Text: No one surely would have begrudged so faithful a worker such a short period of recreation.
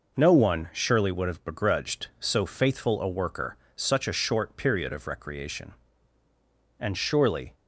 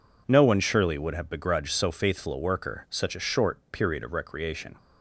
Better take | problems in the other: second | pauses between "worker" and "such"; slight; at 3.5 s; 0.20 s long // goes on to say "And surely"; noticeable; from 6.7 s on; 0.76 s long

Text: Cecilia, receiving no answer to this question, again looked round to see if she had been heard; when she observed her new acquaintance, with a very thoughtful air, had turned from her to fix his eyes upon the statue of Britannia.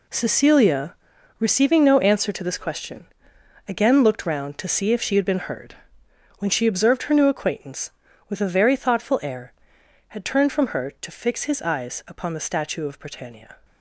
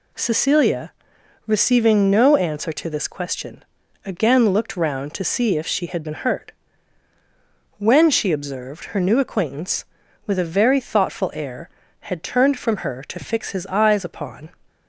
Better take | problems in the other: first | stops before "the statue of Britannia"; at 14.6 s

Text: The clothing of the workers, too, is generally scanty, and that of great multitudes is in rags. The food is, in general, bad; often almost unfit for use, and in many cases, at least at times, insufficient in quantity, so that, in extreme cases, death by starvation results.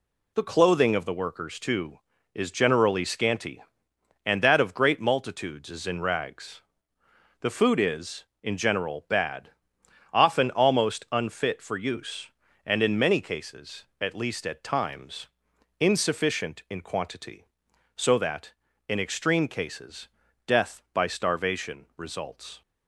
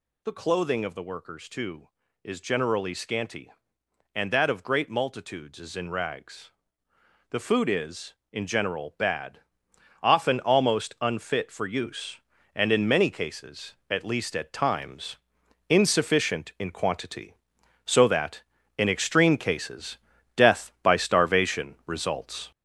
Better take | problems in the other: first | gets louder; noticeable; throughout; 6 dB

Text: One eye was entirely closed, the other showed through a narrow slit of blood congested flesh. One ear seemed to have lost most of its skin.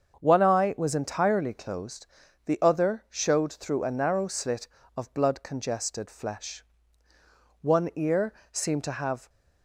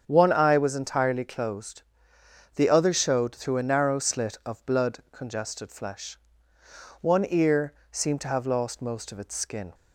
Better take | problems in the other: second | starts louder than the rest; until 1.2 s; 7 dB; strong in the second // pauses between "ear" and "seemed"; slight; at 8.3 s; 0.20 s long; slight in the second // stops before "lost most of its skin"; at 9.2 s

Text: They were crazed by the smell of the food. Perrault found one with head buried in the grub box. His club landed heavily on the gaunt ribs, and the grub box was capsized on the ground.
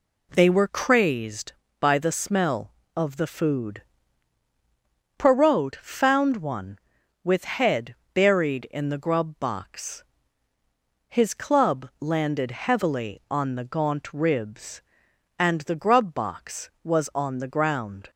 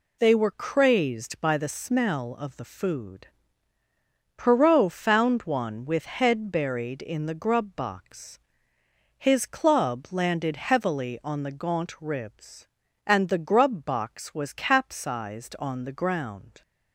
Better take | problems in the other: second | pauses between "head" and "buried"; slight; at 7.9 s; 0.18 s long // skips "capsized"; at 17.1 s

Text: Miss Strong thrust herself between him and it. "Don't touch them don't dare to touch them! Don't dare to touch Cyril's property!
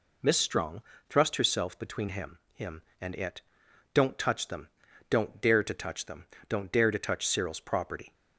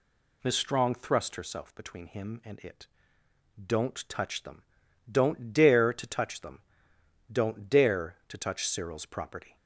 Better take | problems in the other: second | pauses between "Strong" and "thrust"; slight; at 0.8 s; 0.28 s long // says "him" twice; at 2.5 s // pauses between "them" and "don't"; at 4.6 s; 0.40 s long; noticeable in the second

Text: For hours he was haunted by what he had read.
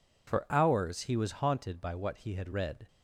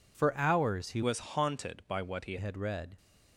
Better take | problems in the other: first | changes voice from "was" to "he"; from 1.0 to 2.3 s; 1.3 s long

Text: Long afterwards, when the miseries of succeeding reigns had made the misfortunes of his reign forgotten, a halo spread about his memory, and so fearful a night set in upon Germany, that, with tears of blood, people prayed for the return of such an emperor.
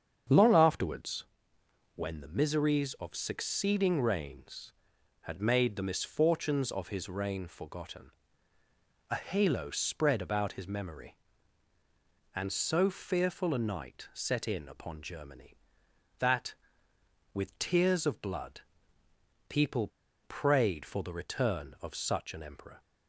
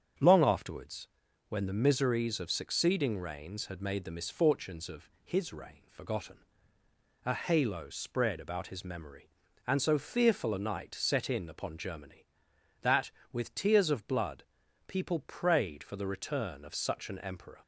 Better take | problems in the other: second | starts louder than the rest; strong; until 2.0 s; 7.5 dB; strong in the second // pauses between "people" and "prayed"; slight; at 19.8 s; 0.35 s long

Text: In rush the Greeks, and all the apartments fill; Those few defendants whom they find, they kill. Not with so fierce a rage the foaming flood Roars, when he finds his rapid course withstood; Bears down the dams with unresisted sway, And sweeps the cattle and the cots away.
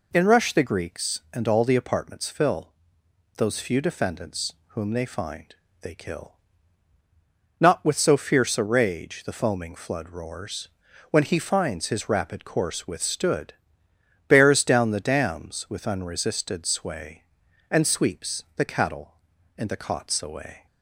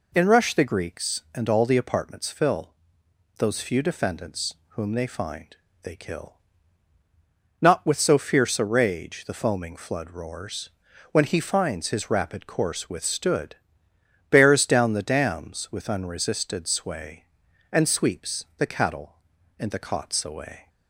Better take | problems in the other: neither | pauses between "defendants" and "whom"; slight; the same in both

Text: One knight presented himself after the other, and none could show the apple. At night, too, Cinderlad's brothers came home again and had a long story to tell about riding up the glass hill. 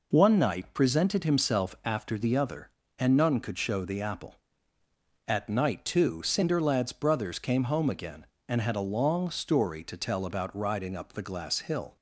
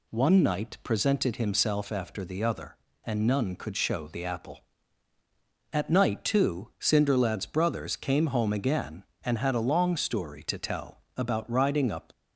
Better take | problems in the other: first | pauses between "tell" and "about"; slight; at 11.0 s; 0.16 s long // stops before "the glass hill"; at 12.1 s

